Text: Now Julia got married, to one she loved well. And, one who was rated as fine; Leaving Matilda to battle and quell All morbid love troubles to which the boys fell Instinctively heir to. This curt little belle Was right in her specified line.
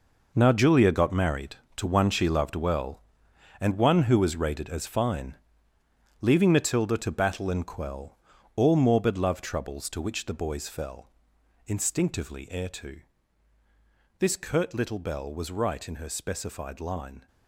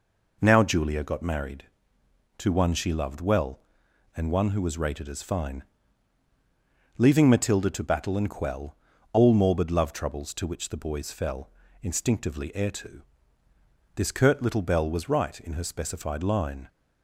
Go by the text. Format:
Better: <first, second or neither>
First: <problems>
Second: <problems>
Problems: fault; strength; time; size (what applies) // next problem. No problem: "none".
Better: second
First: gets quieter; strong; throughout; 11 dB // pauses between "quell" and "All"; at 8.1 s; 0.38 s long // pauses between "fell" and "Instinctively"; noticeable; at 11.1 s; 0.56 s long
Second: pauses between "quell" and "All"; at 8.7 s; 0.38 s long // pauses between "fell" and "Instinctively"; slight; at 11.5 s; 0.32 s long